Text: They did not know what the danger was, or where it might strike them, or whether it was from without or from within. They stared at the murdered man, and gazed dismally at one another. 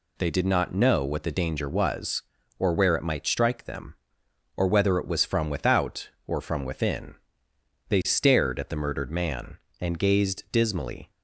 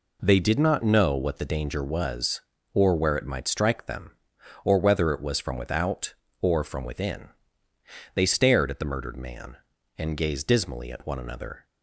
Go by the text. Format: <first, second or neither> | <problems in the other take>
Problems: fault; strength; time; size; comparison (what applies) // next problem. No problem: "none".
second | stops before "at one another"; at 11.1 s